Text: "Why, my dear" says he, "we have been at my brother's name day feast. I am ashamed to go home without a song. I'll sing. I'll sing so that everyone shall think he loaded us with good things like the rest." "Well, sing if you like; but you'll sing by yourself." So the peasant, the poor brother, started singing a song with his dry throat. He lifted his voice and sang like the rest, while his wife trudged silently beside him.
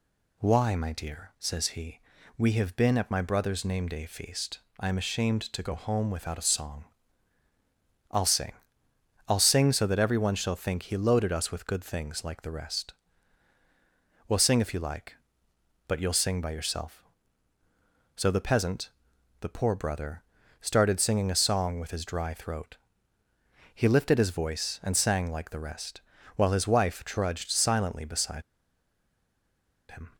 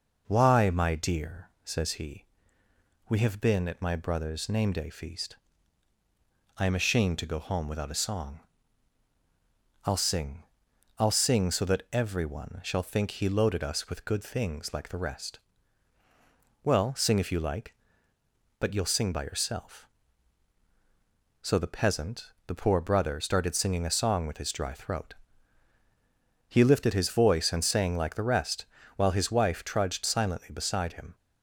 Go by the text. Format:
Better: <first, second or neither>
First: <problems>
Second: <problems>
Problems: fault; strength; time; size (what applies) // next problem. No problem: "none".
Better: second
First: pauses between "beside" and "him"; strong; at 28.4 s; 1.4 s long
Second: none